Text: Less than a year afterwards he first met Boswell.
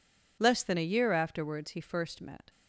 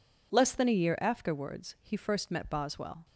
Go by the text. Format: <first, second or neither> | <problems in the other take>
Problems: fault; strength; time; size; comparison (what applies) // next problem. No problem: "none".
second | stops before "Boswell"; at 2.4 s